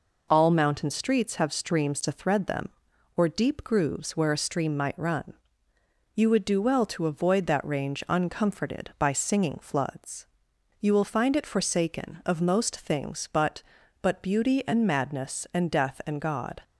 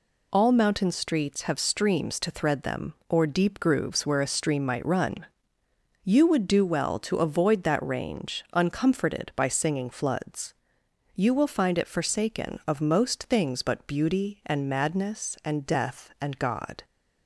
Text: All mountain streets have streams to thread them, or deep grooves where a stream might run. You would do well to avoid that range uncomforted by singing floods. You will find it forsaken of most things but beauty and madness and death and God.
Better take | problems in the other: second | says "but" twice; at 14.0 s

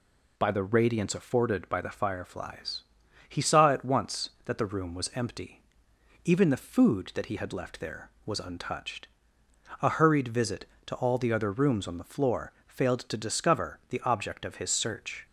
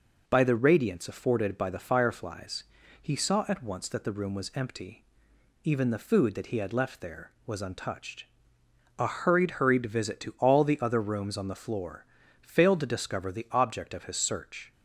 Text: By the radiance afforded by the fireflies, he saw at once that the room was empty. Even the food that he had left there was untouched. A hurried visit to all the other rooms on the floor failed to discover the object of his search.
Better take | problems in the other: first | says "hurried" twice; at 9.5 s // pauses between "floor" and "failed"; slight; at 12.0 s; 0.36 s long; slight in the first

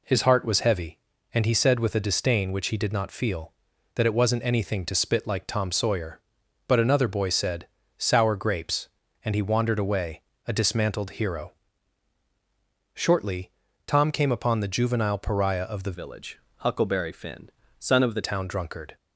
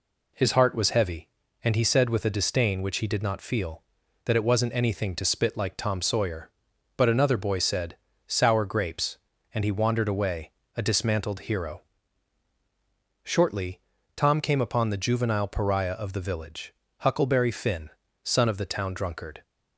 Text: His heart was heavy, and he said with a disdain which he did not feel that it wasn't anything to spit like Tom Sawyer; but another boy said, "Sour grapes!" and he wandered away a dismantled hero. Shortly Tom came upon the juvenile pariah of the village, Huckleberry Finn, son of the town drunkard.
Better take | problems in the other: second | pauses between "away" and "a"; slight; at 10.2 s; 0.24 s long; slight in the second // pauses between "Shortly" and "Tom"; slight; at 13.5 s; 0.36 s long; slight in the second // changes voice from "village" to "the"; from 15.9 to 18.2 s; 2.3 s long

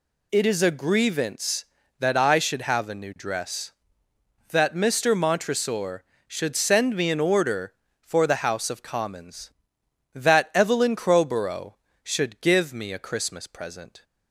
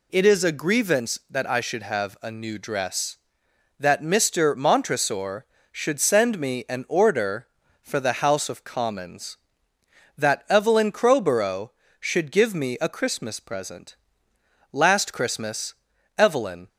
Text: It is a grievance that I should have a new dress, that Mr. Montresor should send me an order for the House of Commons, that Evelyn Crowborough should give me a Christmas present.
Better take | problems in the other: first | goes on to say "Last Christmas Evelyn"; strong; from 14.7 s on; 1.9 s long

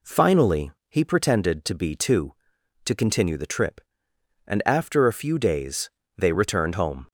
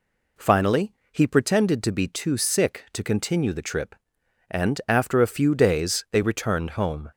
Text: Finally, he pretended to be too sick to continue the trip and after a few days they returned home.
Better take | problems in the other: second | skips "sick"; at 2.5 s // pauses between "days" and "they"; slight; at 5.8 s; 0.28 s long

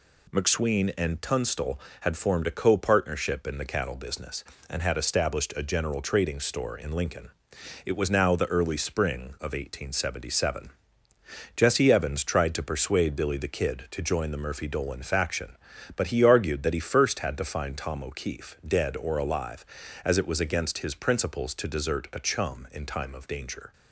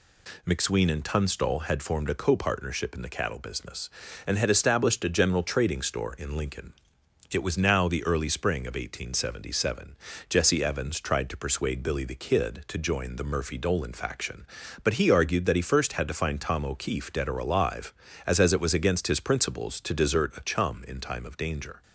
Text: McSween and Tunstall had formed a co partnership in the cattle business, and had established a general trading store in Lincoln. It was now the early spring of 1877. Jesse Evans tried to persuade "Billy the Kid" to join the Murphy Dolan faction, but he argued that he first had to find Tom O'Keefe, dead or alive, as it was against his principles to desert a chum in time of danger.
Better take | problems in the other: first | says "as" twice; at 18.3 s

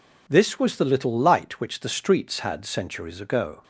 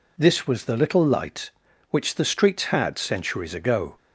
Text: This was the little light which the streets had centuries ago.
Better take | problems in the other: neither | none

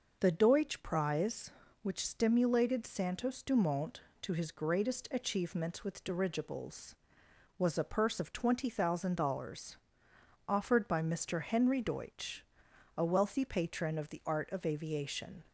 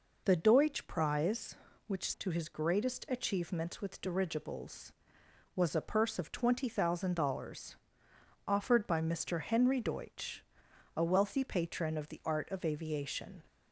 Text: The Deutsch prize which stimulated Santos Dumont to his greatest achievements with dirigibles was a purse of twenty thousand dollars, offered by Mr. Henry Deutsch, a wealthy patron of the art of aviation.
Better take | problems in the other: first | skips "stimulated Santos Dumont"; at 2.1 s

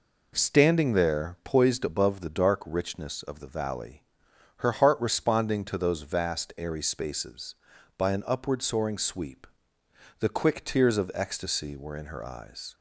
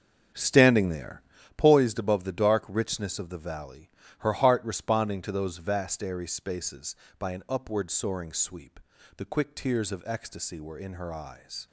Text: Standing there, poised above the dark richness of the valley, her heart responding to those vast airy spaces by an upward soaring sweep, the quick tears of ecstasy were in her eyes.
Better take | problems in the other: first | starts louder than the rest; strong; until 1.5 s; 7.5 dB

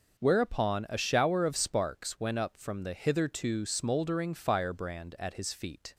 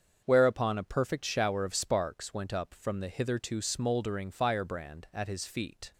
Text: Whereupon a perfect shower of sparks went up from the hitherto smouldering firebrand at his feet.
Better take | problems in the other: second | starts louder than the rest; noticeable; until 1.2 s; 6 dB; also in the second // skips "perfect"; at 0.9 s

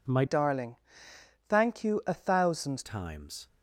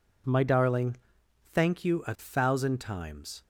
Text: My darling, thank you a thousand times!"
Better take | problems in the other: second | changes voice from "darling" to "thousand"; from 0.2 to 2.8 s; 2.6 s long

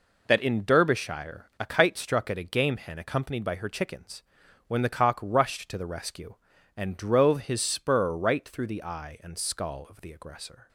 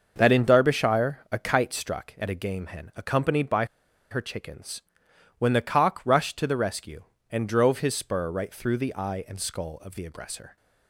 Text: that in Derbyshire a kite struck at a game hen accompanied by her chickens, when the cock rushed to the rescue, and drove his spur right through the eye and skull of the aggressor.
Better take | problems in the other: first | starts louder than the rest; until 1.1 s; 6 dB // pauses between "by" and "her"; noticeable; at 3.6 s; 0.45 s long

